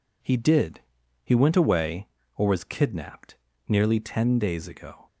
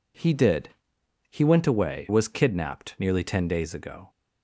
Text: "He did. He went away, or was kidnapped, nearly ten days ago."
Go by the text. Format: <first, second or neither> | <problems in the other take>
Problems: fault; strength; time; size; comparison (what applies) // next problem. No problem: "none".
first | skips "or"; at 2.0 s